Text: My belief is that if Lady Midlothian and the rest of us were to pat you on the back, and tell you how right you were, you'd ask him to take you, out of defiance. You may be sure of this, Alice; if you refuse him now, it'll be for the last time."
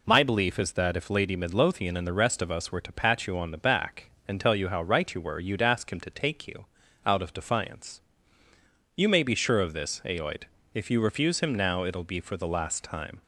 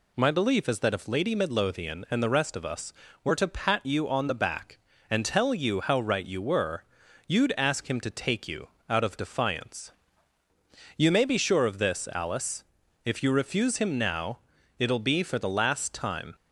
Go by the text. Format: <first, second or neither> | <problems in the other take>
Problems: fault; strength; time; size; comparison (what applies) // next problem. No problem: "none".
second | says "Aoid" for "Alice"; at 10.0 s